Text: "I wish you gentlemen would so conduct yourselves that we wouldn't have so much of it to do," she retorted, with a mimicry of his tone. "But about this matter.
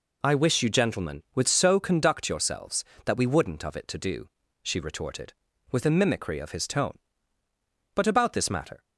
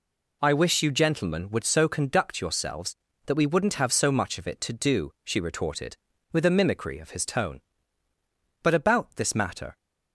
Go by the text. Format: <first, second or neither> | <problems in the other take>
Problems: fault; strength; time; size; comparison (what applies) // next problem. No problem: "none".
second | skips "have so much"; at 3.6 s